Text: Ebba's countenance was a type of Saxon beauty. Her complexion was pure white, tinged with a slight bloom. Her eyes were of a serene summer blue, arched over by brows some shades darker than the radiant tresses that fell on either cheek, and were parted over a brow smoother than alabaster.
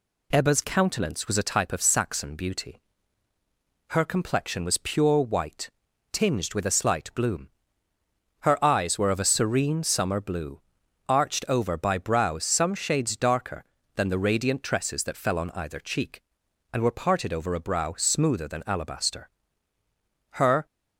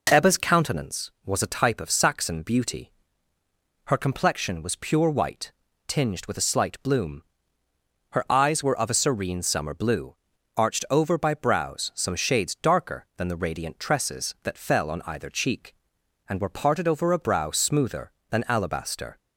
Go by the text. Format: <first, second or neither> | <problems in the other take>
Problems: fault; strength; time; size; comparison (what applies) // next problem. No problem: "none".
second | goes on to say "Her"; slight; from 20.3 s on; 0.34 s long